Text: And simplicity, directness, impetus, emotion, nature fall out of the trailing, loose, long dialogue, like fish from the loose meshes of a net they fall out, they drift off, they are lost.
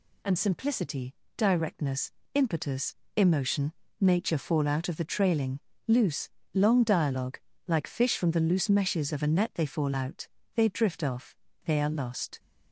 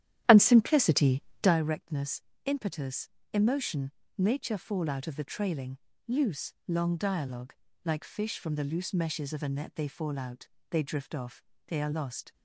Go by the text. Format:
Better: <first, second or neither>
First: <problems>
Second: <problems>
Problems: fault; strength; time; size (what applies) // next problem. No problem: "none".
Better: first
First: none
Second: starts louder than the rest; strong; until 1.6 s; 11.5 dB